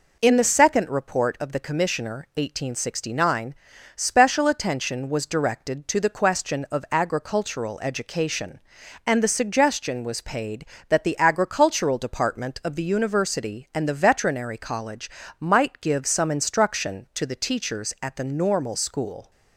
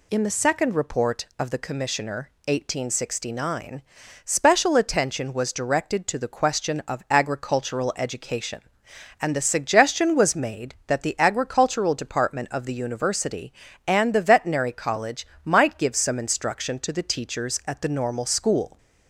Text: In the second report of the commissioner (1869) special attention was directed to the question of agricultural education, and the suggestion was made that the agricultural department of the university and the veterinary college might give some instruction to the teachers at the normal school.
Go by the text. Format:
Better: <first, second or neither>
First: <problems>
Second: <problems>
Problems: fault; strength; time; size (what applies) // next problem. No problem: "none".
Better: second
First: says "paid" for "made"; at 10.2 s // pauses between "college" and "might"; slight; at 15.0 s; 0.30 s long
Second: pauses between "college" and "might"; slight; at 15.2 s; 0.18 s long